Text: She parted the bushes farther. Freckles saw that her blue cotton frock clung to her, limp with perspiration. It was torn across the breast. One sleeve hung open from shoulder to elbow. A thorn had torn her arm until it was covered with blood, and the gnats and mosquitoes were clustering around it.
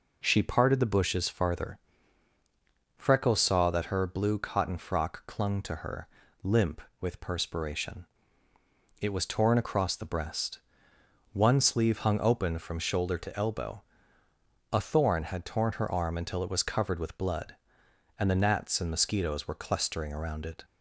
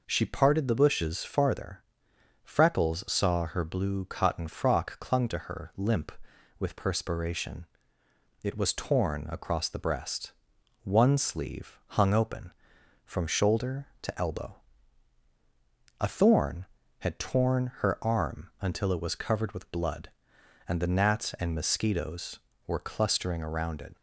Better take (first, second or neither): first